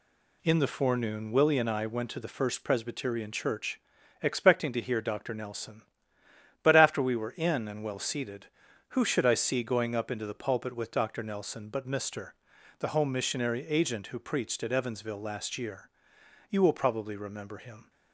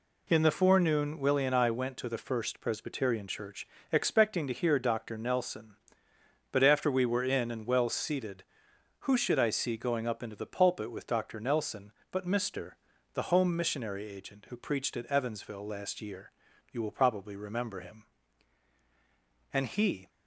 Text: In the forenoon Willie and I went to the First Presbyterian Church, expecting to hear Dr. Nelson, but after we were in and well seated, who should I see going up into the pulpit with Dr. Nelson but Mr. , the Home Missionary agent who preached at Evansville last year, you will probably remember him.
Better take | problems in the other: first | goes on to say "And he"; from 19.5 s on; 0.58 s long

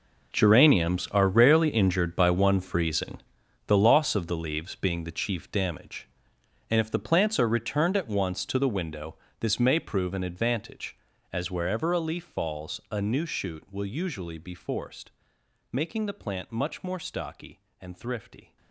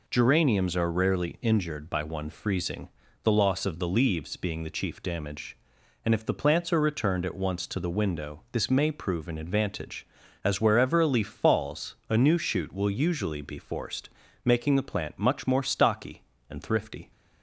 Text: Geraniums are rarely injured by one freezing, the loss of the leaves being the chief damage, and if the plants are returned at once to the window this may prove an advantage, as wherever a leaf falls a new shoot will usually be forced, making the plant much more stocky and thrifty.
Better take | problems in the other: second | gets quieter; strong; throughout; 15.5 dB // pauses between "window" and "this"; slight; at 9.1 s; 0.26 s long

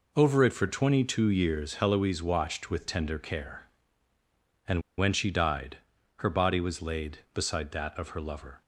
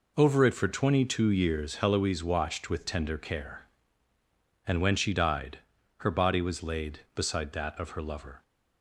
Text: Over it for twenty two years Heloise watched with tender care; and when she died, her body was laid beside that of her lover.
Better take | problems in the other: second | pauses between "and" and "when"; slight; at 4.8 s; 0.17 s long

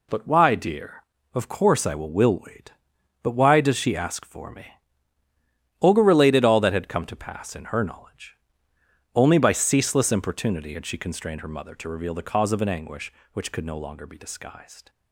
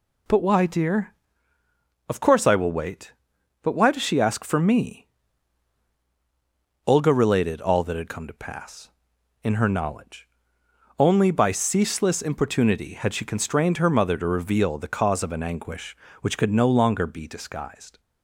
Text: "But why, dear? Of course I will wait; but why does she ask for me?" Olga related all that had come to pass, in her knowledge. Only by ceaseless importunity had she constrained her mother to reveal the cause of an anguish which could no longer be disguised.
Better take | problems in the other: second | says "will" twice; at 2.0 s

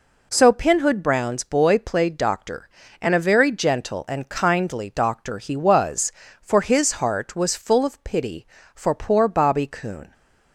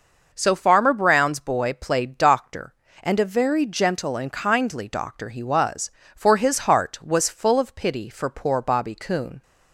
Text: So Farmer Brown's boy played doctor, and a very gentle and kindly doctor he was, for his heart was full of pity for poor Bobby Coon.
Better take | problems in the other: second | says "Pinhood" for "Farmer"; at 0.5 s

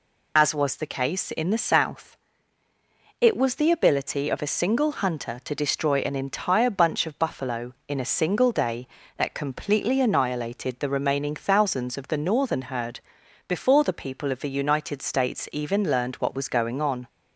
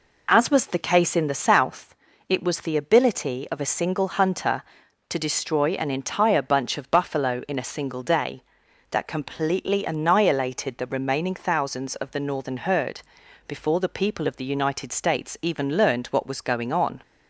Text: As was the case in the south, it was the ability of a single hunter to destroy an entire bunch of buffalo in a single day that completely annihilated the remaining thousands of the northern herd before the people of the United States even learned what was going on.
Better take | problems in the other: second | loses the start of "As"; at 0.3 s; 40 ms // pauses between "herd" and "before"; noticeable; at 12.9 s; 0.48 s long; noticeable in the second

